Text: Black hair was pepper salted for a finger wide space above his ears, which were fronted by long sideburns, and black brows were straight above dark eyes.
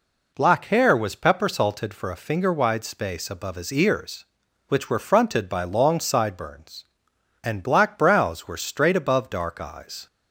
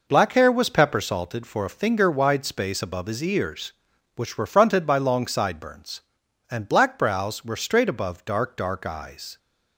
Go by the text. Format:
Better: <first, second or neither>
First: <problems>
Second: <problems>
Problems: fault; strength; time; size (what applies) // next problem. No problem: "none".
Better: first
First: none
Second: says "dark" twice; at 8.5 s